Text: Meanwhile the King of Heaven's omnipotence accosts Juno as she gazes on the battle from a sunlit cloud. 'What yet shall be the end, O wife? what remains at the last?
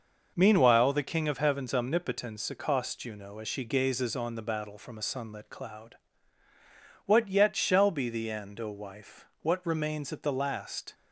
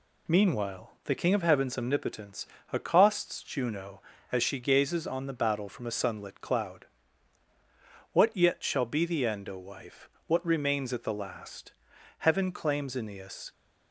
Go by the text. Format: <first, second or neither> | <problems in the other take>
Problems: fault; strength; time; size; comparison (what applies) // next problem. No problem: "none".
first | pauses between "omnipotence" and "accosts"; slight; at 2.4 s; 0.26 s long // goes on to say "Heaven claims Aeneas"; from 12.1 s on; 1.3 s long